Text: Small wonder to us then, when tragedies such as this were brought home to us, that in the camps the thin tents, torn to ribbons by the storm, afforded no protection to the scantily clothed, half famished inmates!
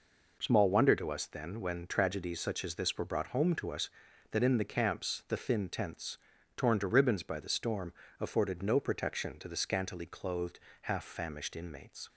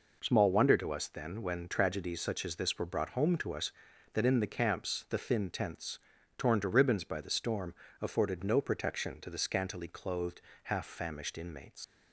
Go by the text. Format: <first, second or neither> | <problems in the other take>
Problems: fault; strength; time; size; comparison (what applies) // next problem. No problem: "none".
first | leaves "inmates" unfinished; at 11.8 s; 55 ms